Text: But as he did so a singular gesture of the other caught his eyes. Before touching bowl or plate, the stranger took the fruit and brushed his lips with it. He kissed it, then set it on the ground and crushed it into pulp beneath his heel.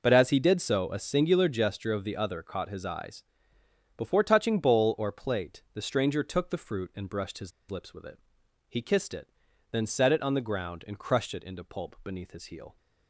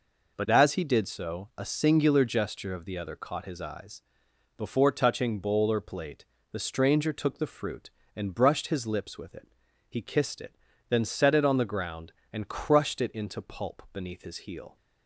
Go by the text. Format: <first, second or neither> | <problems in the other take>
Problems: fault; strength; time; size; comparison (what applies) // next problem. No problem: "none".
second | pauses between "his" and "lips"; slight; at 7.5 s; 0.19 s long